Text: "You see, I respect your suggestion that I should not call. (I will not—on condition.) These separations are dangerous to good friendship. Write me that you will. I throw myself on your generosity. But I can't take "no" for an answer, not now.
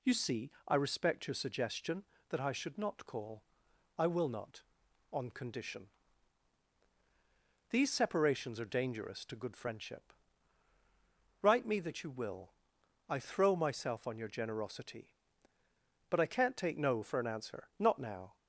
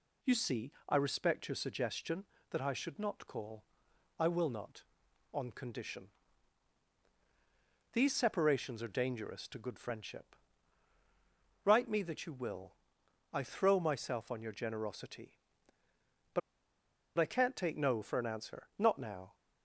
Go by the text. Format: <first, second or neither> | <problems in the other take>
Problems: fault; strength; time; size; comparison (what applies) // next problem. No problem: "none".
first | pauses between "But" and "I"; noticeable; at 16.4 s; 0.78 s long